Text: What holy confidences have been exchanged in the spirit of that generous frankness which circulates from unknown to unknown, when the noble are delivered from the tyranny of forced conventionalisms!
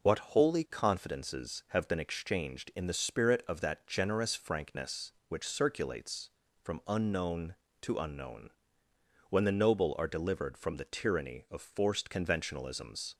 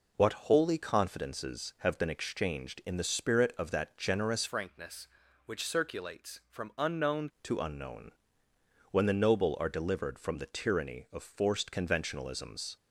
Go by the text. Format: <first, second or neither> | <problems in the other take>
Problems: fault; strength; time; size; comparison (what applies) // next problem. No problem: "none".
first | changes voice from "frankness" to "unknown"; from 4.4 to 7.3 s; 2.9 s long